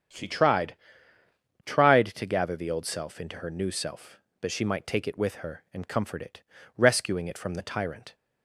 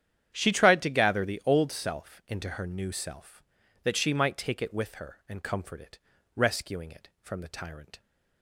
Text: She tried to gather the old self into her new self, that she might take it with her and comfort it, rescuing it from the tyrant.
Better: second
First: starts louder than the rest; strong; until 2.0 s; 8.5 dB // says "tried" twice; at 1.6 s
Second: starts louder than the rest; strong; until 1.3 s; 9.5 dB

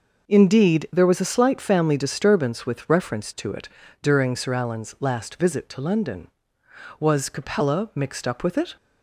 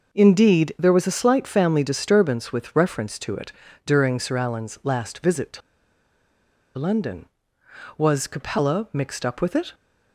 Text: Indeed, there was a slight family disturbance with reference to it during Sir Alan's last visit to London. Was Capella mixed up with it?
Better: first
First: pauses between "it" and "during"; slight; at 3.6 s; 0.34 s long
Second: pauses between "it" and "during"; slight; at 3.5 s; 0.34 s long // pauses between "to" and "London"; at 5.6 s; 1.1 s long

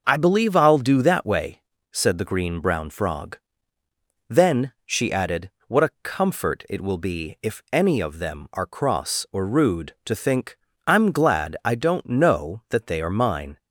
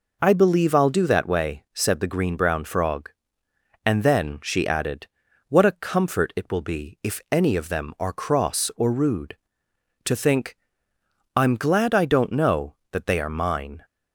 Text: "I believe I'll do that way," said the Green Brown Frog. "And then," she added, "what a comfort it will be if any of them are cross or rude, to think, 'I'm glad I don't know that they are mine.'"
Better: second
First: starts louder than the rest; noticeable; until 1.0 s; 6 dB // skips "And"; at 3.8 s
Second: none

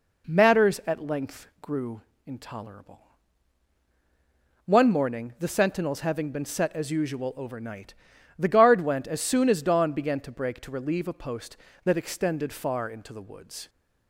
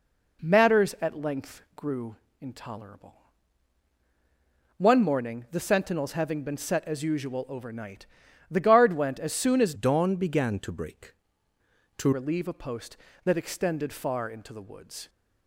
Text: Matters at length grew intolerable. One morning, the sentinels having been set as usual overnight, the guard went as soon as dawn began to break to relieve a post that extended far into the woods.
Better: first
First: pauses between "grew" and "intolerable"; slight; at 2.0 s; 0.24 s long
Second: pauses between "grew" and "intolerable"; slight; at 2.1 s; 0.24 s long // changes voice from "dawn" to "to"; from 9.7 to 12.1 s; 2.4 s long

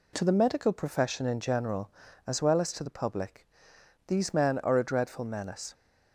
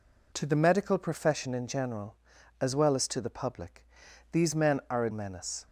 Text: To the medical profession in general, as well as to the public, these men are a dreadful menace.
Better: first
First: none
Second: skips "dreadful"; at 5.1 s

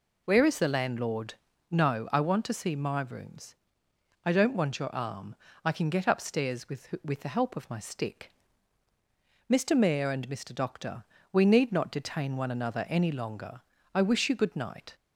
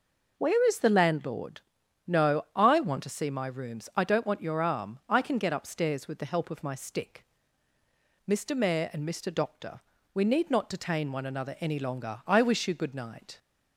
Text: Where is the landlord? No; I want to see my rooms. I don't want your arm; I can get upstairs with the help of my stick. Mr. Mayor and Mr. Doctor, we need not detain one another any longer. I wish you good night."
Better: second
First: says "with" twice; at 7.0 s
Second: none

